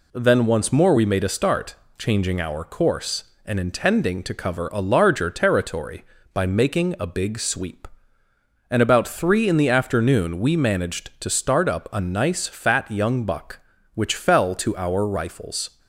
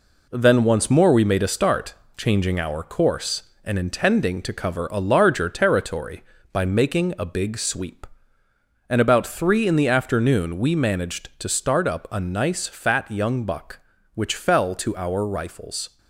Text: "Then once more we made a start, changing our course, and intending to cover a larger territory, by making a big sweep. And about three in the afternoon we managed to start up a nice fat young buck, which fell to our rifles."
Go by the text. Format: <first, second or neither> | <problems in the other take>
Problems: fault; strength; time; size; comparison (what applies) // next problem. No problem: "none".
first | gets quieter; throughout; 6.5 dB